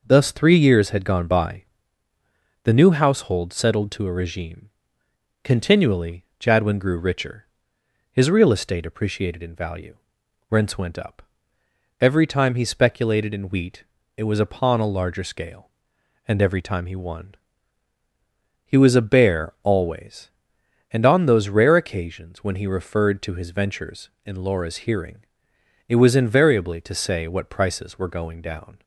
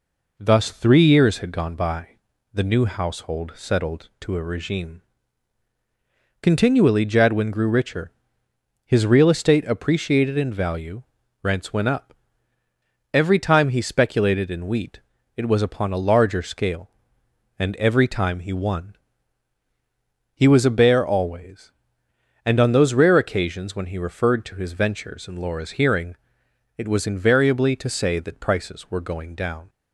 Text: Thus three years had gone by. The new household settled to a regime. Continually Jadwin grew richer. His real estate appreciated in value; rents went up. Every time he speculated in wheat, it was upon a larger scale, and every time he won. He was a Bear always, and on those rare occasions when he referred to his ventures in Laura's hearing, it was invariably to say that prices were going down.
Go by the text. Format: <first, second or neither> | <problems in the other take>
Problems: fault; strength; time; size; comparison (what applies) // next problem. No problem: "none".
second | pauses between "Continually" and "Jadwin"; slight; at 6.2 s; 0.16 s long // says "what" for "that"; at 27.2 s